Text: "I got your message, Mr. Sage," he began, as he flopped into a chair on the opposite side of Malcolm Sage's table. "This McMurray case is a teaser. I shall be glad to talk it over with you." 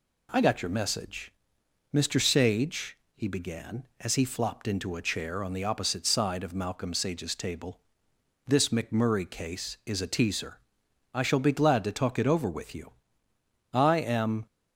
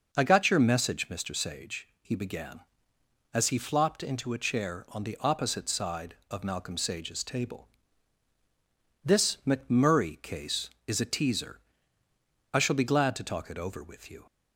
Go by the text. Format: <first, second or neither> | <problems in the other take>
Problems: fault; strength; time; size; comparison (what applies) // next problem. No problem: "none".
second | goes on to say "I am"; noticeable; from 13.7 s on; 0.72 s long